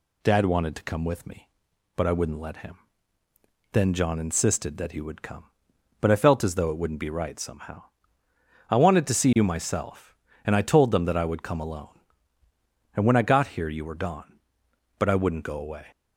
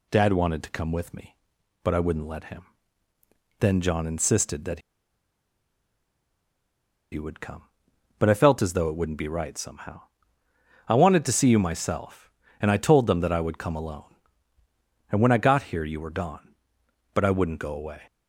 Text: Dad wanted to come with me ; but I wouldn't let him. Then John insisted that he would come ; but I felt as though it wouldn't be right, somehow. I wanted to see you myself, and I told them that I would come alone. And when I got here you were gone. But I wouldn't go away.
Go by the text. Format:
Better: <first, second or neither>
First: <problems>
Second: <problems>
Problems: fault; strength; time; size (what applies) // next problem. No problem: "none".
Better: first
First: none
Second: pauses between "that" and "he"; strong; at 4.7 s; 2.3 s long